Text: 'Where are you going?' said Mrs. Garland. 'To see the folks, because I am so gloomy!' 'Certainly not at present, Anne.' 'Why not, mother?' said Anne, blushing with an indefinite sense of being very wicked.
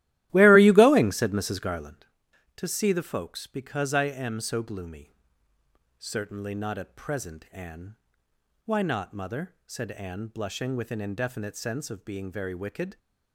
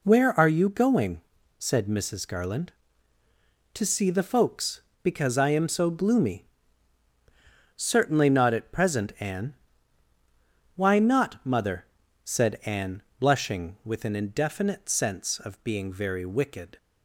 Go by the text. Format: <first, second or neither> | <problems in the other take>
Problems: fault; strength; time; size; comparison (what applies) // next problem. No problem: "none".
second | starts louder than the rest; strong; until 2.1 s; 15 dB